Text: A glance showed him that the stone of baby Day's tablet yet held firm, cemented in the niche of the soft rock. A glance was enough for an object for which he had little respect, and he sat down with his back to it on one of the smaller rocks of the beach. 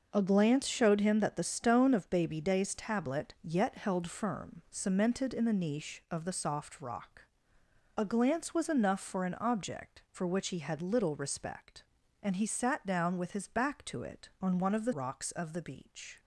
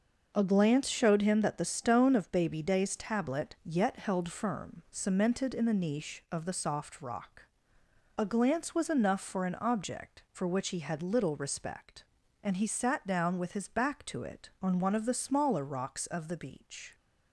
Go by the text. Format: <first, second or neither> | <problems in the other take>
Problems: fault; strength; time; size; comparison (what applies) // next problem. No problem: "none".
second | starts louder than the rest; noticeable; until 1.1 s; 6 dB; noticeable in the second // skips "smaller"; at 14.9 s